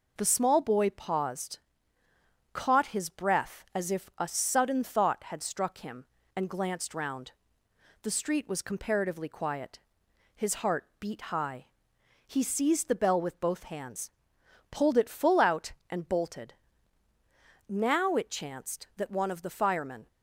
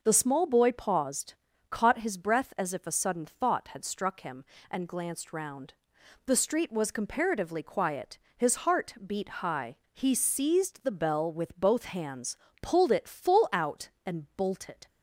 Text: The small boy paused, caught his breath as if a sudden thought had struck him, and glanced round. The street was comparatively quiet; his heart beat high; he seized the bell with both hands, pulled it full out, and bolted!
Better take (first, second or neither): second